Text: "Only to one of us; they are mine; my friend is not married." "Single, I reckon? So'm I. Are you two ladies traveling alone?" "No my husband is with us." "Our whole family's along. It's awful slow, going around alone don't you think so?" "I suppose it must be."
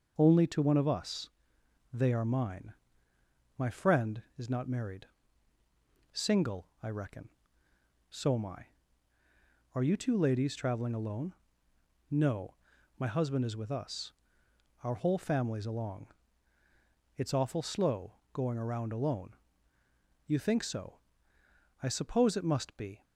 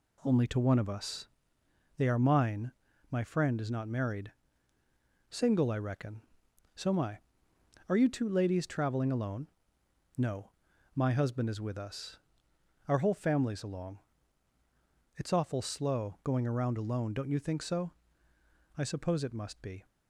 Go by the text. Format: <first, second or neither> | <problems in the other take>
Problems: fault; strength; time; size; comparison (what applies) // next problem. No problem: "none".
second | pauses between "No" and "my"; at 12.5 s; 0.44 s long; also in the second // skips "don't"; at 19.8 s